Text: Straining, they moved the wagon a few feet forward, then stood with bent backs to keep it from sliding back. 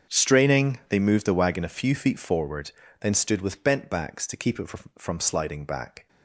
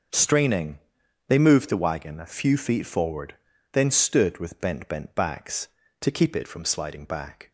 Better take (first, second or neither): first